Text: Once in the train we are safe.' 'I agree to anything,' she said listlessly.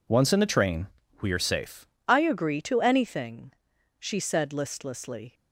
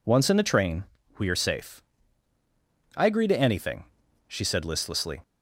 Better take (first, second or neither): second